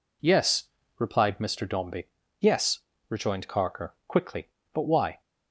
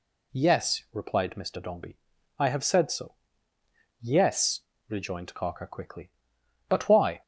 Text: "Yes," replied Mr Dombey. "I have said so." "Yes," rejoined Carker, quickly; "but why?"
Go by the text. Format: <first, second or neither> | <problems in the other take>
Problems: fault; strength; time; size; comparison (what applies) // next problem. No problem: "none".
second | skips "I have said so"; at 2.2 s